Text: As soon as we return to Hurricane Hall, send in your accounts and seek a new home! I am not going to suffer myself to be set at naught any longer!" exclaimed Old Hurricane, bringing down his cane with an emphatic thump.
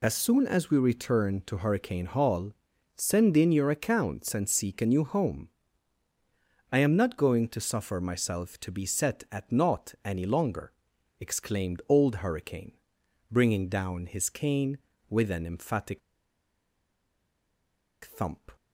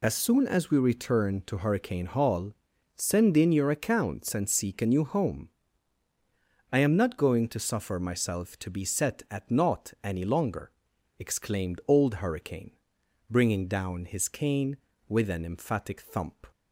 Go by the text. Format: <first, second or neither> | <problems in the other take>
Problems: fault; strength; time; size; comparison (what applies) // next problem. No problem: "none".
second | pauses between "emphatic" and "thump"; strong; at 16.0 s; 2.0 s long